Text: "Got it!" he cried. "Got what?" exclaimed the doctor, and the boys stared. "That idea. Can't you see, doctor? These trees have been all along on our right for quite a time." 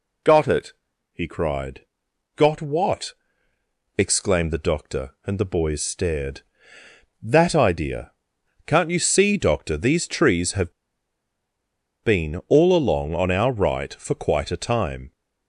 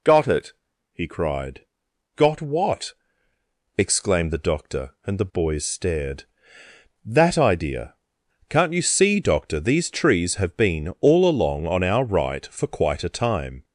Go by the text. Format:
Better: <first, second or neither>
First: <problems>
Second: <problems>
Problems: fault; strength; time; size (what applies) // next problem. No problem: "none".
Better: second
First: pauses between "have" and "been"; strong; at 10.7 s; 1.3 s long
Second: none